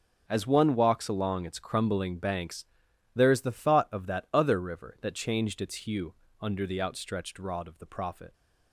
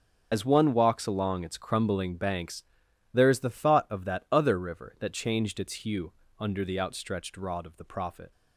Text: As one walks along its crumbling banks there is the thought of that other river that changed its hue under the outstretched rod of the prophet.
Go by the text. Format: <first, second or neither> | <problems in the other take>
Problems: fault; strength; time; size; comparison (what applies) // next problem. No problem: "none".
first | loses the start of "As"; at 0.3 s; 50 ms // starts louder than the rest; until 1.3 s; 7 dB; also in the first // pauses between "banks" and "there"; noticeable; at 2.6 s; 0.50 s long; noticeable in the first // pauses between "hue" and "under"; slight; at 6.1 s; 0.26 s long; slight in the first